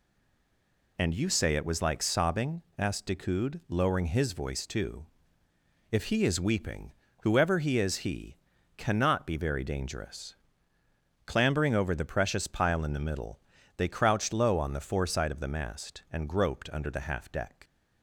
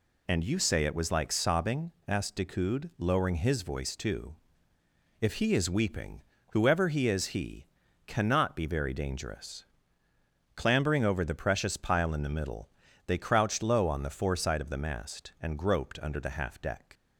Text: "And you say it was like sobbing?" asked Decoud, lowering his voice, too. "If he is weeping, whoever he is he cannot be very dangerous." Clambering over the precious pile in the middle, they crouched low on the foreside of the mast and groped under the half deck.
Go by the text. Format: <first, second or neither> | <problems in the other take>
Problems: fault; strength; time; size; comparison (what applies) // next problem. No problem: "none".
second | stays silent before the first word; until 0.9 s; 0.9 s long // pauses between "he" and "cannot"; at 8.3 s; 0.40 s long; also in the second